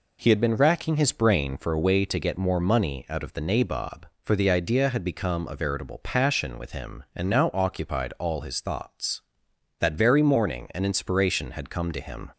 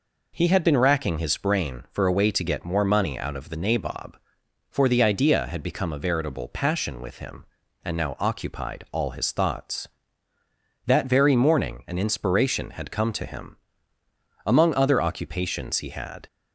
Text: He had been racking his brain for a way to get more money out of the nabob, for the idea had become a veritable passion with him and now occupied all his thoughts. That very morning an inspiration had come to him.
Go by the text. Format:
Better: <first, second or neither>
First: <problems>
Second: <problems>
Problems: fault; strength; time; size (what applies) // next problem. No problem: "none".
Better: first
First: none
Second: goes on to say "Among other occupations he had"; strong; from 14.4 s on; 1.8 s long